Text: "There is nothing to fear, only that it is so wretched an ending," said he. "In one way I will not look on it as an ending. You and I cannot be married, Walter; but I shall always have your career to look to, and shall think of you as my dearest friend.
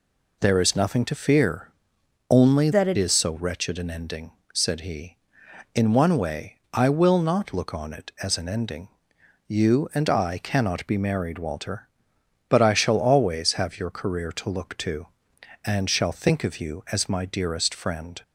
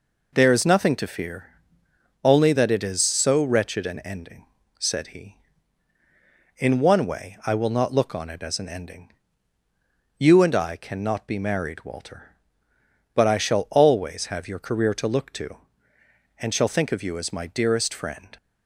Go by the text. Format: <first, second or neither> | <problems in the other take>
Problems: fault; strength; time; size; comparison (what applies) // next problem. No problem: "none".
second | changes voice from "that" to "it"; from 2.7 to 2.9 s; 0.2 s long